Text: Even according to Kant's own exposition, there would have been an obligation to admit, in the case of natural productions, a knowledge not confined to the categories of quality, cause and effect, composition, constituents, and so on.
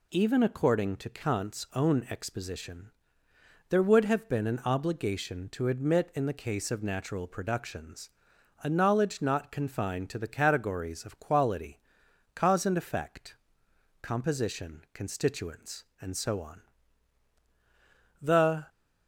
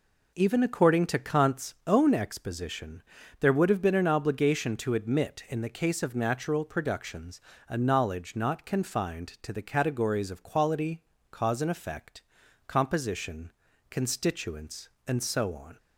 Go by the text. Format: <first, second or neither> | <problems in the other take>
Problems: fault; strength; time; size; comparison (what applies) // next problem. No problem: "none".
second | goes on to say "The"; slight; from 18.2 s on; 0.46 s long